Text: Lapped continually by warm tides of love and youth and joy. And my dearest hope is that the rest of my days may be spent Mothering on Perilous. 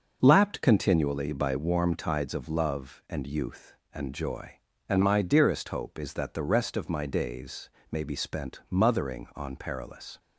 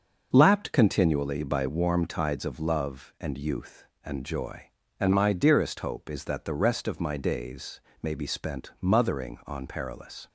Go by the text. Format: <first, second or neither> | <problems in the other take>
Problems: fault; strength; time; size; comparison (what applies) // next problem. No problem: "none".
neither | starts louder than the rest; noticeable; the same in both // pauses between "days" and "may"; slight; the same in both